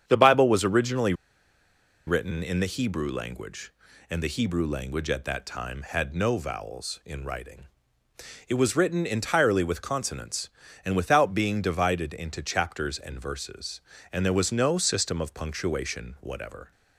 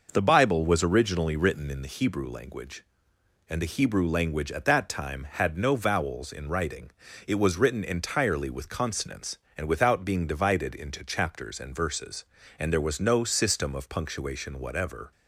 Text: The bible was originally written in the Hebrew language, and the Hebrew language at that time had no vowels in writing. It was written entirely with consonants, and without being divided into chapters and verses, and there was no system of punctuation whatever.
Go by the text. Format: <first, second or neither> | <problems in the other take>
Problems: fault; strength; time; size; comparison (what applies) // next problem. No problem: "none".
second | starts louder than the rest; strong; until 1.0 s; 8.5 dB // pauses between "originally" and "written"; noticeable; at 1.1 s; 0.93 s long